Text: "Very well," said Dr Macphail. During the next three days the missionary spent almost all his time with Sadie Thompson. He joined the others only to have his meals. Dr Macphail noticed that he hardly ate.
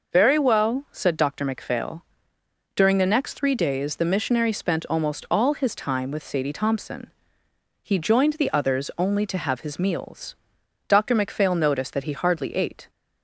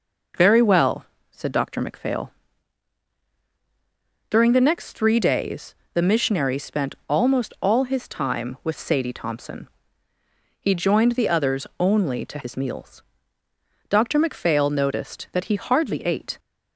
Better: first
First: none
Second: pauses between "days" and "the"; slight; at 5.7 s; 0.18 s long // skips "have"; at 12.3 s

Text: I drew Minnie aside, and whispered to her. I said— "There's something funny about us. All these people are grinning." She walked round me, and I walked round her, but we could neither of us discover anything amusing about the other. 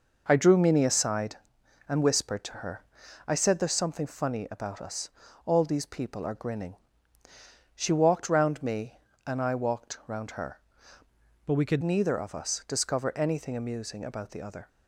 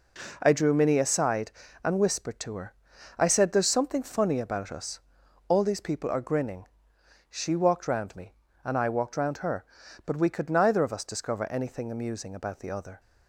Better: second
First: changes voice from "but" to "could"; from 11.4 to 11.8 s; 0.4 s long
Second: none

